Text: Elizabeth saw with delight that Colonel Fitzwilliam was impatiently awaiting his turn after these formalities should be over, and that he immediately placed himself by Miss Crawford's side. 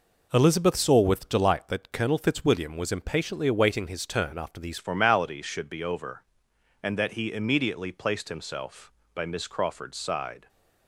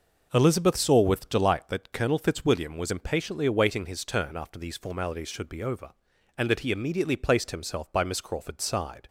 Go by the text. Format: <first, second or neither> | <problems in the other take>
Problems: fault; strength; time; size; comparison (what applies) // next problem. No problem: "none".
second | changes voice at "formalities"; from 4.7 s on; 5.7 s long